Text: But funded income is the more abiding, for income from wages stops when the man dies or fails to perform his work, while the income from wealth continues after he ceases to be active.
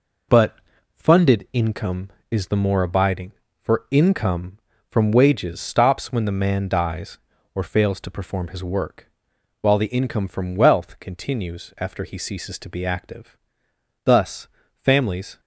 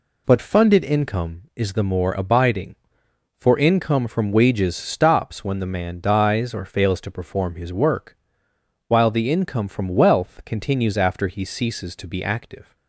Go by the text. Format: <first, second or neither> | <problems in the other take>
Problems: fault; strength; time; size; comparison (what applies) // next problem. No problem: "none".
second | pauses between "But" and "funded"; slight; at 0.5 s; 0.36 s long // goes on to say "Thus families"; from 14.0 s on; 1.3 s long